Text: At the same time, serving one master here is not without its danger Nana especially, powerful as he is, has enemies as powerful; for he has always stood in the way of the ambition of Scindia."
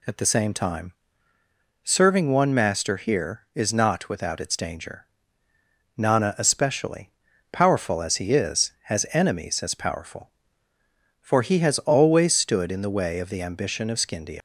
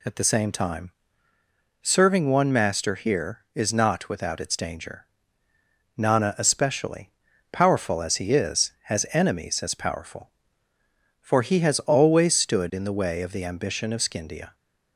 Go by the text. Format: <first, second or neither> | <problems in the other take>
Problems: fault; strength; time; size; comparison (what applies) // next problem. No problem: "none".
second | pauses between "danger" and "Nana"; noticeable; at 5.0 s; 0.90 s long; noticeable in the second // leaves "Scindia" unfinished; at 14.3 s; 115 ms